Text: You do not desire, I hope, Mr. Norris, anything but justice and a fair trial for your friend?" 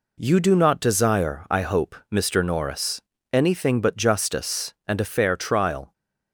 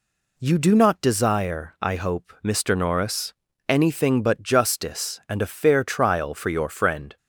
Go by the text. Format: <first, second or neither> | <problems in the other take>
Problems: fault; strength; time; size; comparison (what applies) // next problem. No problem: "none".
second | stops before "for your friend"; at 5.9 s